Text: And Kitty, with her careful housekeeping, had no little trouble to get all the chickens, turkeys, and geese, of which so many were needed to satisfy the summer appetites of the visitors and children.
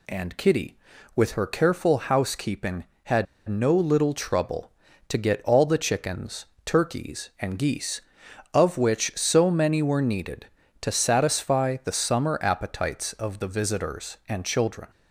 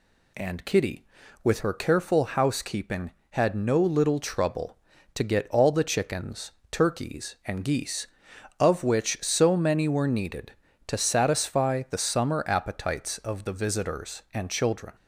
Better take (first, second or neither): second